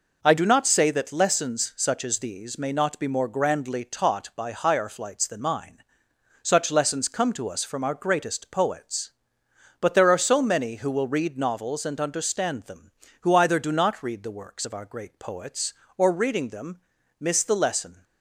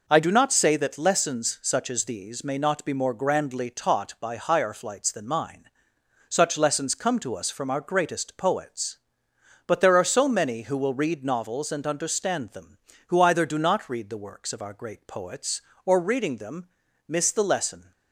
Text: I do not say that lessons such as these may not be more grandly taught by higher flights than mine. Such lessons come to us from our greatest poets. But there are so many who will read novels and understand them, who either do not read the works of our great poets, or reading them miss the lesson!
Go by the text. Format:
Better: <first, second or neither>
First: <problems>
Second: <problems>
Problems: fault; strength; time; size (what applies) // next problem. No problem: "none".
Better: neither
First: pauses between "them" and "miss"; at 16.7 s; 0.40 s long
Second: pauses between "them" and "miss"; at 16.6 s; 0.40 s long